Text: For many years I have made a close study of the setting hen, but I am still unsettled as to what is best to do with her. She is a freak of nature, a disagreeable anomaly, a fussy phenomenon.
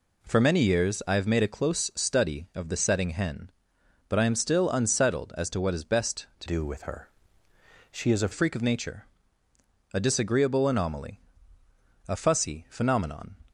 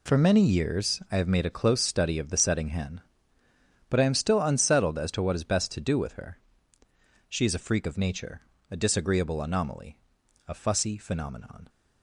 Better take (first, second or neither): second